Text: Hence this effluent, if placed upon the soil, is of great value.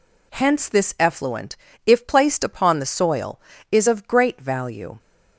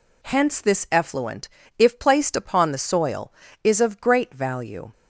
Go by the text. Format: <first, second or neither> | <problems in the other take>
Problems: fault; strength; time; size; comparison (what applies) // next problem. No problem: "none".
neither | none